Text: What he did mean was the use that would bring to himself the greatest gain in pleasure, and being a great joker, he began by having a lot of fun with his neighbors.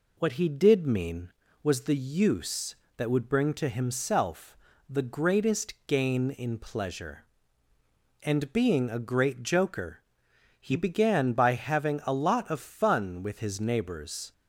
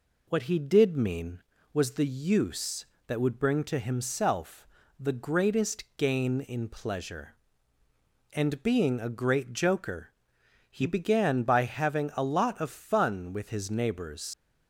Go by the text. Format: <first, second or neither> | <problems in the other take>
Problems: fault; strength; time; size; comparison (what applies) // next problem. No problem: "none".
first | pauses between "himself" and "the"; slight; at 4.6 s; 0.34 s long; slight in the first // leaves "neighbors" unfinished; at 14.3 s; 90 ms